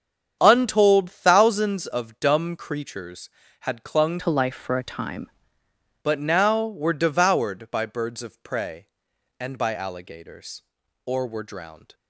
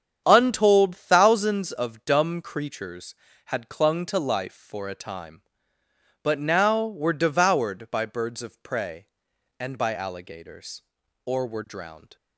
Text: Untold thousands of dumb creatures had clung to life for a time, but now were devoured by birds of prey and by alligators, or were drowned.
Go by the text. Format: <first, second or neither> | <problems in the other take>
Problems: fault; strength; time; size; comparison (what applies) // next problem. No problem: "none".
second | starts louder than the rest; strong; until 1.4 s; 8 dB; strong in the second // changes voice from "to" to "time"; from 4.1 to 5.3 s; 1.2 s long